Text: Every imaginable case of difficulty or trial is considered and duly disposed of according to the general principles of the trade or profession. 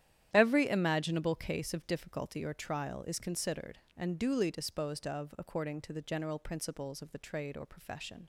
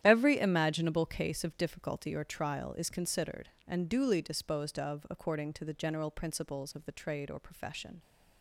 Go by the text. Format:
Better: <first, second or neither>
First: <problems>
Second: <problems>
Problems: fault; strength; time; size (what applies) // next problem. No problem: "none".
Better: neither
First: starts louder than the rest; strong; until 1.3 s; 11 dB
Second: starts louder than the rest; strong; until 1.0 s; 11 dB